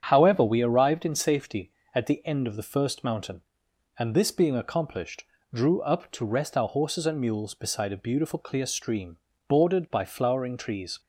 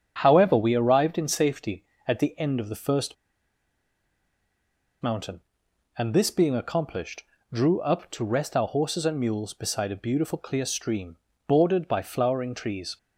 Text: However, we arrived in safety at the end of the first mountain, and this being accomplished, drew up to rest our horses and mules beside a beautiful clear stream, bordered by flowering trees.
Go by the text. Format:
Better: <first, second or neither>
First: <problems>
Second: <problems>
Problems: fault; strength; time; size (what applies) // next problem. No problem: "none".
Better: first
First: starts louder than the rest; strong; until 1.0 s; 8.5 dB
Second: starts louder than the rest; strong; until 1.2 s; 8 dB // pauses between "first" and "mountain"; strong; at 3.1 s; 1.8 s long